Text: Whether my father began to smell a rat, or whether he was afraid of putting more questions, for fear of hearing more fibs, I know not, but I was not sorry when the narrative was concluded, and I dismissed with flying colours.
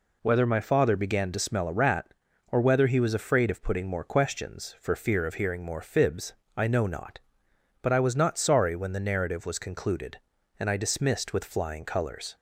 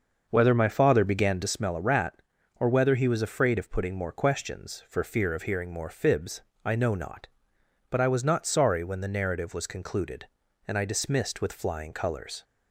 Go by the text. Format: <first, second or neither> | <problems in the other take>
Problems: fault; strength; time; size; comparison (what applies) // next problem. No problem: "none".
first | starts louder than the rest; until 1.6 s; 6 dB